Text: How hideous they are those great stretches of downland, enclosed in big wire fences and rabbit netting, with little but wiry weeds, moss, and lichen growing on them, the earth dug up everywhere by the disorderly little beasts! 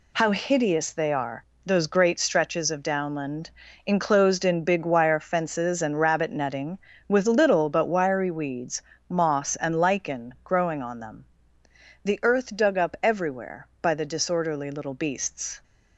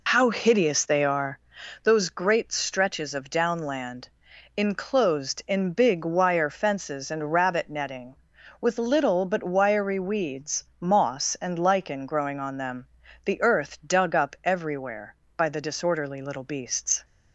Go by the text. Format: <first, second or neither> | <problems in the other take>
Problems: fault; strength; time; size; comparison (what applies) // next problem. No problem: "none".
first | loses the start of "How"; at 0.0 s; 40 ms // pauses between "are" and "those"; noticeable; at 1.3 s; 0.46 s long; slight in the first